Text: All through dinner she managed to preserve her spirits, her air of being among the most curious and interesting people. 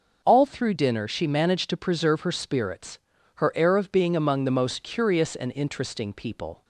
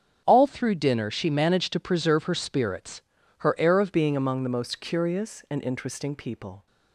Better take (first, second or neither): first